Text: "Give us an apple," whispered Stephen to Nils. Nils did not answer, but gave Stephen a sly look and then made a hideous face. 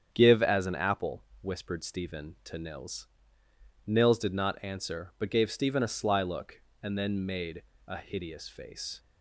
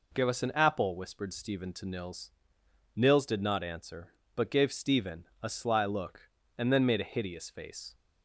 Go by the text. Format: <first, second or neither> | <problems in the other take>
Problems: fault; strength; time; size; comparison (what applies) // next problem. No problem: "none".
second | starts louder than the rest; strong; until 1.1 s; 8.5 dB // says "as" for "us"; at 0.4 s // pauses between "made" and "a"; slight; at 7.6 s; 0.24 s long